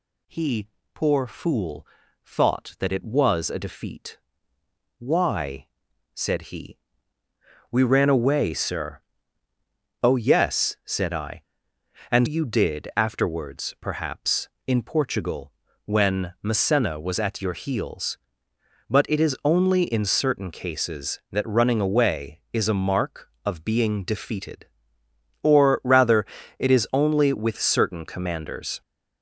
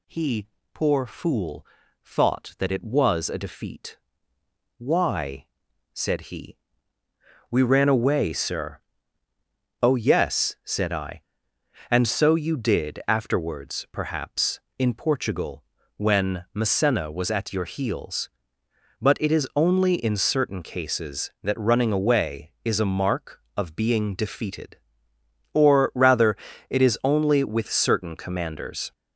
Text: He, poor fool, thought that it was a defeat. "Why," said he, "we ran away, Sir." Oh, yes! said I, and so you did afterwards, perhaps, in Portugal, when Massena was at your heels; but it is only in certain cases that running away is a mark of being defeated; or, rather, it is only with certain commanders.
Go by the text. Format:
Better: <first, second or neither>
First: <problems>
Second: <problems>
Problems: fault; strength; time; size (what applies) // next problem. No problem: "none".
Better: second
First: skips "so"; at 12.2 s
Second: none